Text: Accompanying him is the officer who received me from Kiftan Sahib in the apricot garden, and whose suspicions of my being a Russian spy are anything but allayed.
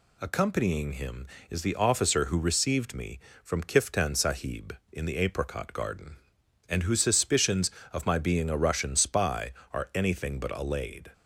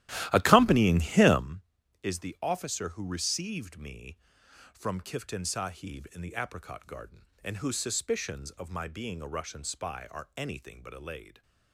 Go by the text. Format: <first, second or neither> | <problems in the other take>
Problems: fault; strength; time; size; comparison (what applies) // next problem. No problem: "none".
first | starts louder than the rest; strong; until 1.5 s; 14.5 dB